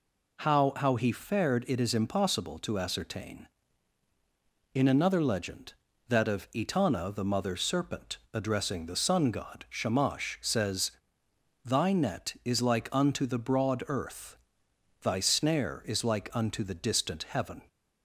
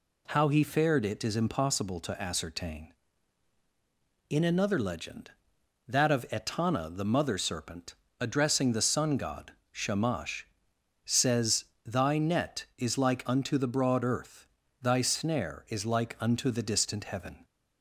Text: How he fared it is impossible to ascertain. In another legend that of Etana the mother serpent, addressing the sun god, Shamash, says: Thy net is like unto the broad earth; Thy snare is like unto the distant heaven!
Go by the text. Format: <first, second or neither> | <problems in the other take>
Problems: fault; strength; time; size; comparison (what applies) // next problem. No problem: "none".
second | says "How" twice; at 0.7 s